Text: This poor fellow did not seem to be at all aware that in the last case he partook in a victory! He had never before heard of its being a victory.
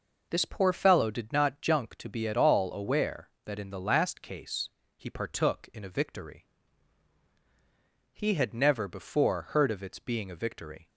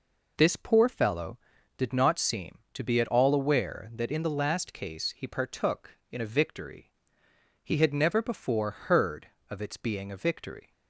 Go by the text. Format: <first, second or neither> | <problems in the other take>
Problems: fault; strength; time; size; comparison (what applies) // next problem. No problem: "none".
second | says "junk" for "seem"; at 1.6 s // pauses between "case" and "he"; slight; at 4.6 s; 0.28 s long